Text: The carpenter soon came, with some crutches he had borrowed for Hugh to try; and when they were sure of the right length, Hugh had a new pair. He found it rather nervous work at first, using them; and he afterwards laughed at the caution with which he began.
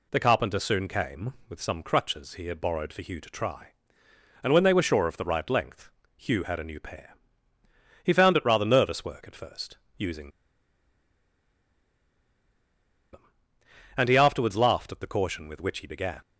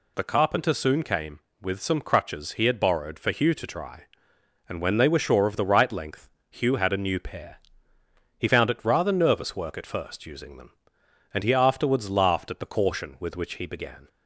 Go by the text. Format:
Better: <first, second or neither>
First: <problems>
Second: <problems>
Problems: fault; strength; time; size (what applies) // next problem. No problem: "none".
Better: second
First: pauses between "using" and "them"; strong; at 10.2 s; 2.8 s long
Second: none